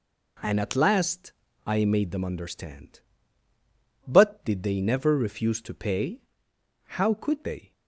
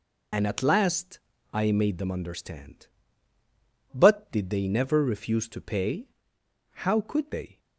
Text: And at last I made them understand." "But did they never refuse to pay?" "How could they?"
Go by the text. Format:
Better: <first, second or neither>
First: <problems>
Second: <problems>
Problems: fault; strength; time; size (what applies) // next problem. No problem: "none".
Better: first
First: pauses between "last" and "I"; slight; at 1.3 s; 0.34 s long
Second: loses the start of "And"; at 0.3 s; 70 ms // pauses between "last" and "I"; slight; at 1.1 s; 0.34 s long